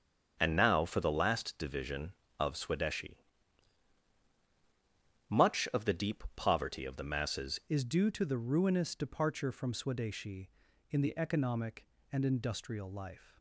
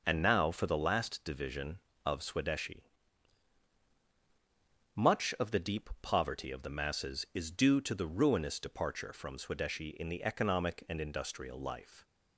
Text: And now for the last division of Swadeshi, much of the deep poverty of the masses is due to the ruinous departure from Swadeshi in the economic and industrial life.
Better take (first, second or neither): second